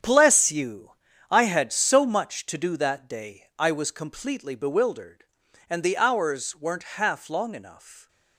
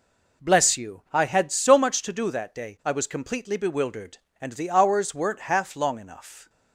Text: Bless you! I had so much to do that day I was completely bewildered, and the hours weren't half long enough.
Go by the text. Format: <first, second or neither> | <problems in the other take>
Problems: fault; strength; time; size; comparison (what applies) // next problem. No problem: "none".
second | gets quieter; strong; throughout; 11.5 dB